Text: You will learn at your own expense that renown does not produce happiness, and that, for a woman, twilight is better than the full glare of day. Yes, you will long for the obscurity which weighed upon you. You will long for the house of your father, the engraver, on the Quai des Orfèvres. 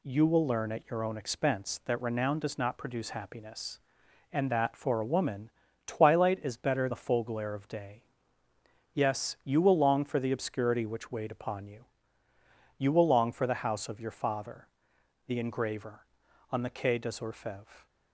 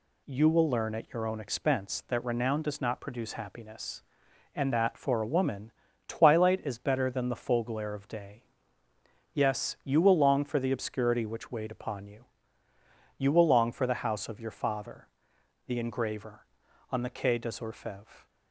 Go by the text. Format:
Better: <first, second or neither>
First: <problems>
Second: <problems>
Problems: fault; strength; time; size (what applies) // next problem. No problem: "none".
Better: second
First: skips "than"; at 6.8 s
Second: none